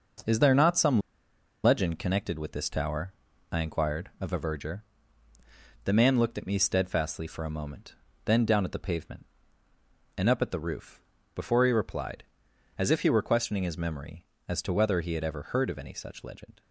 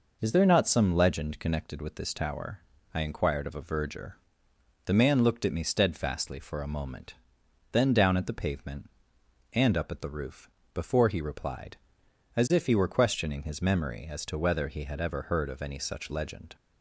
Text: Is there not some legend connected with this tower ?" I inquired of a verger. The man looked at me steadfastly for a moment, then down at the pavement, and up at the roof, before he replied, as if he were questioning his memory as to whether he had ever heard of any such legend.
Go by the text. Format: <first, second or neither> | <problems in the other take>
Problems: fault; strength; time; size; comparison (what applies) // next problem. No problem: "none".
second | pauses between "some" and "legend"; noticeable; at 0.9 s; 0.65 s long